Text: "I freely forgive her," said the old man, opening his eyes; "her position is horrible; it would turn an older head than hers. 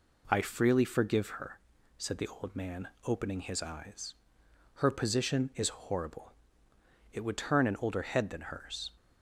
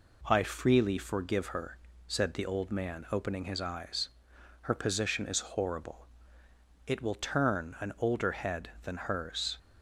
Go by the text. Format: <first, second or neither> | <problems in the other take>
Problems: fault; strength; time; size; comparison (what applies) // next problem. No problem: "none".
first | says "will" for "would"; at 7.0 s